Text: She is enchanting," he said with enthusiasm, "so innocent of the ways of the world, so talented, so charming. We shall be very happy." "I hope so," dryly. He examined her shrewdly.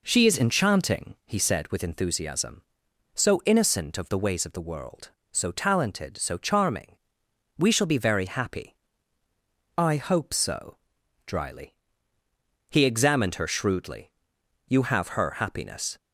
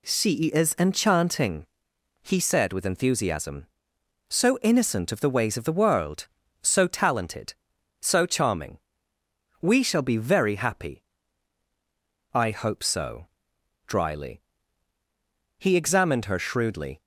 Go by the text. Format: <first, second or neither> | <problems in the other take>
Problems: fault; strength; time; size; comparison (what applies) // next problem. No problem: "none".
second | goes on to say "You have her happiness"; noticeable; from 14.6 s on; 1.3 s long